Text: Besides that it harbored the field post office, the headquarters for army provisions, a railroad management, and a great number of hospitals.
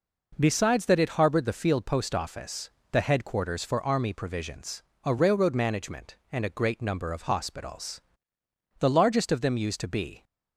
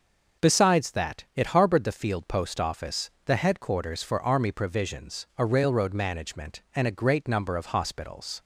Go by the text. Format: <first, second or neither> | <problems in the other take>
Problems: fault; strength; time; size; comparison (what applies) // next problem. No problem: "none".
second | goes on to say "The largest of them used to be"; from 8.7 s on; 1.4 s long